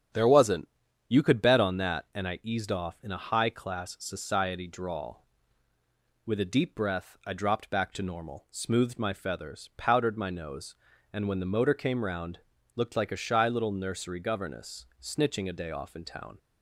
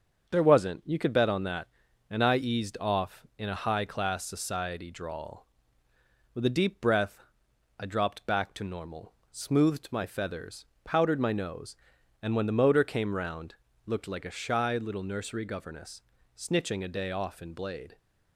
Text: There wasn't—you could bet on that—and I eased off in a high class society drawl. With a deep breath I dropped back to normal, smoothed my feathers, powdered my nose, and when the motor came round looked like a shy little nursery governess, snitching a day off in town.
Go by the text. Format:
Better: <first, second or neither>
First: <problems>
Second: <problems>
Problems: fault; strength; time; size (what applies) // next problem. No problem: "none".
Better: first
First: starts louder than the rest; strong; until 1.5 s; 8 dB // pauses between "round" and "looked"; at 12.3 s; 0.38 s long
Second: starts louder than the rest; until 1.3 s; 7 dB // pauses between "breath" and "I"; noticeable; at 7.2 s; 0.56 s long // pauses between "round" and "looked"; slight; at 13.5 s; 0.30 s long // says "blade" for "town"; at 17.5 s